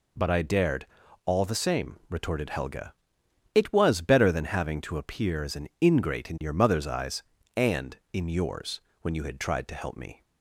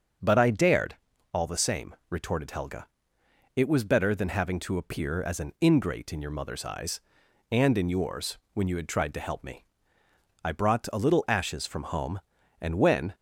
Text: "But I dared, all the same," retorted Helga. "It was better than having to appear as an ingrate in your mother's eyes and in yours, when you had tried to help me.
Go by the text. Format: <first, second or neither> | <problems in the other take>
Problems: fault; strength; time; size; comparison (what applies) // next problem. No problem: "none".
first | starts louder than the rest; until 1.6 s; 6.5 dB // goes on to say "I brought a little ashes from home and when"; strong; from 10.4 s on; 2.7 s long